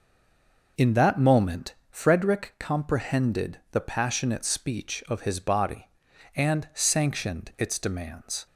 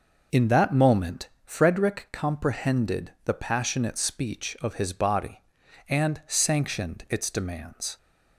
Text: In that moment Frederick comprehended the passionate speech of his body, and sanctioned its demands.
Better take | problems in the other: second | stays silent before the first word; slight; until 0.7 s; 0.7 s long // pauses between "moment" and "Frederick"; slight; at 1.7 s; 0.16 s long; slight in the second

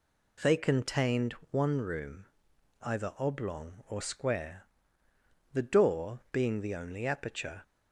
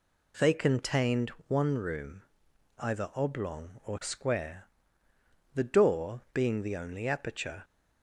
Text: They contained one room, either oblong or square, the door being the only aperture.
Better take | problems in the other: neither | pauses between "contained" and "one"; slight; the same in both

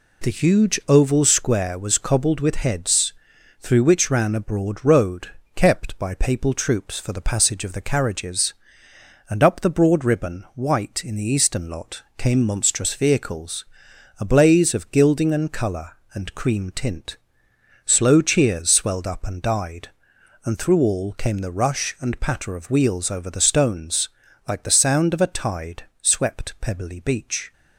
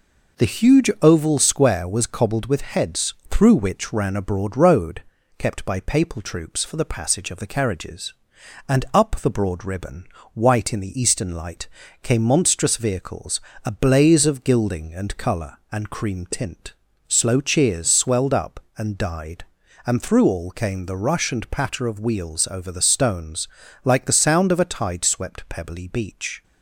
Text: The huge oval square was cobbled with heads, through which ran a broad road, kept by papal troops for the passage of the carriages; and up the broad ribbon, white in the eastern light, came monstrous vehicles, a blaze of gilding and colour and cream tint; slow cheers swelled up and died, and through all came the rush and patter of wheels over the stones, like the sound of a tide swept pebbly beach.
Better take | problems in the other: second | says "lot" for "light"; at 11.6 s // pauses between "tide" and "swept"; slight; at 25.8 s; 0.18 s long

